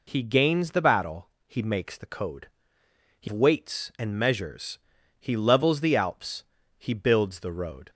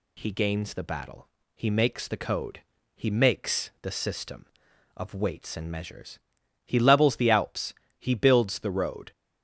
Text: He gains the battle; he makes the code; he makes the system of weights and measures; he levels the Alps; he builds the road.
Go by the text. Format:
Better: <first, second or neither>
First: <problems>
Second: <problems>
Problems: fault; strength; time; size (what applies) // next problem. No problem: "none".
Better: second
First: skips "makes the system of"; at 3.2 s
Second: none